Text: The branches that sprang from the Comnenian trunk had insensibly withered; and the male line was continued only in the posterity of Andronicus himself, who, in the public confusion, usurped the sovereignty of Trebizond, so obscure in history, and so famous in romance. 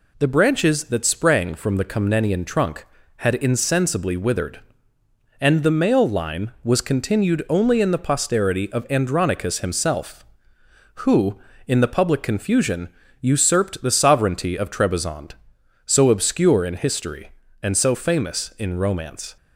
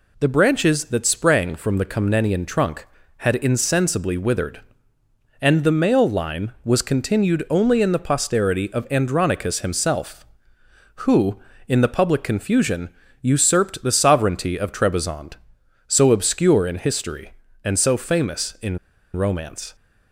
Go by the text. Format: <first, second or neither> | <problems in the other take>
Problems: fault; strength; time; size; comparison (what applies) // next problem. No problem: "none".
first | pauses between "in" and "romance"; at 18.7 s; 0.36 s long